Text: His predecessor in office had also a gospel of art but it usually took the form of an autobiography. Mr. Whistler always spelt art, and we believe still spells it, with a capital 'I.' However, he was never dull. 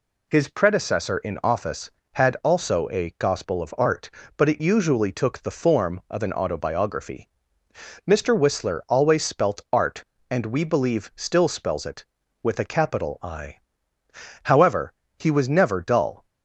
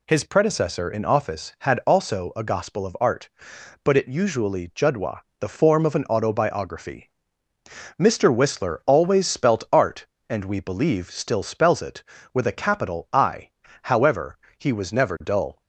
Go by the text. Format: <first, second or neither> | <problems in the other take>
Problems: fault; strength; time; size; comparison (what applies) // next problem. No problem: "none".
first | says "judwa" for "took"; at 4.7 s